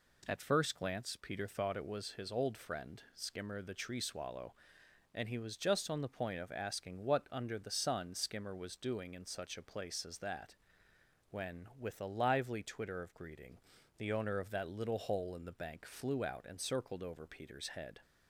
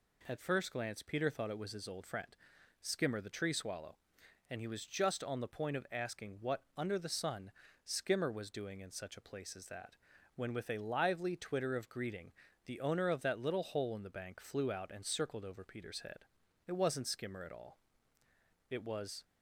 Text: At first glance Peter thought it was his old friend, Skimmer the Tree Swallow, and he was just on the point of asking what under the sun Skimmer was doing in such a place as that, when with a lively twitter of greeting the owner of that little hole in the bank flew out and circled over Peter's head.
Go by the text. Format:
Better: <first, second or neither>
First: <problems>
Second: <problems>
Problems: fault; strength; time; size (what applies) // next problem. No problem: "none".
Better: first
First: pauses between "greeting" and "the"; at 13.5 s; 0.38 s long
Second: pauses between "sun" and "Skimmer"; slight; at 7.5 s; 0.32 s long // pauses between "greeting" and "the"; slight; at 12.3 s; 0.34 s long // goes on to say "It wasn't Skimmer at all It was"; strong; from 16.6 s on; 2.5 s long